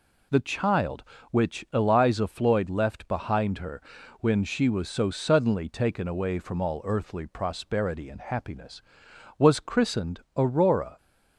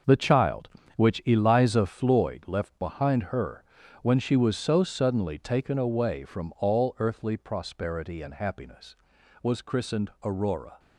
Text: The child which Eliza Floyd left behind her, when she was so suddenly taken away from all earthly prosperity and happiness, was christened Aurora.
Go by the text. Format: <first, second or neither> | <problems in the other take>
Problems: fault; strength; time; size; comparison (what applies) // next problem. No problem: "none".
first | gets quieter; strong; throughout; 9.5 dB